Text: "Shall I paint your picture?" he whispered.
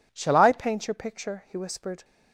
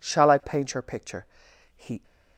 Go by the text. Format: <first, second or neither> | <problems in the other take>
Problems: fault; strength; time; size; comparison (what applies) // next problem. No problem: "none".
first | stops before "whispered"; at 2.0 s